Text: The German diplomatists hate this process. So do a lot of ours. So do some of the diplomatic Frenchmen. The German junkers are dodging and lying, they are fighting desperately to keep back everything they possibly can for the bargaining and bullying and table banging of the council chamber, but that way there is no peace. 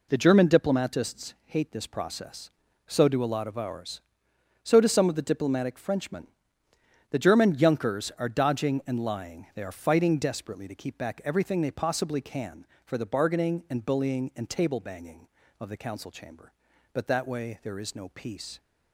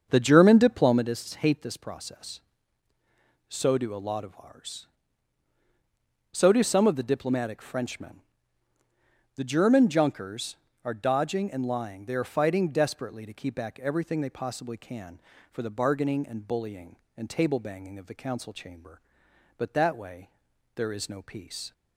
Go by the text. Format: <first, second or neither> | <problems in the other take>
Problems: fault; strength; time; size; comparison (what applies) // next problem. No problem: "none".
first | starts louder than the rest; until 1.1 s; 7 dB // pauses between "way" and "there"; noticeable; at 20.3 s; 0.46 s long